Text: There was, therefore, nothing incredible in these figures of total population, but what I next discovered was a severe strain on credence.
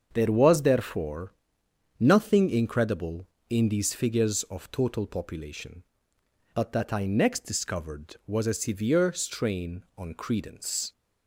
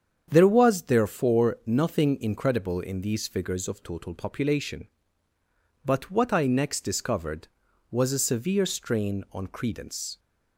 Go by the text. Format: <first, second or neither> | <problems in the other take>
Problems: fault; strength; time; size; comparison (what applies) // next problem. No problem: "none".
second | starts louder than the rest; until 1.1 s; 7 dB; strong in the second // says "that" for "what"; at 6.7 s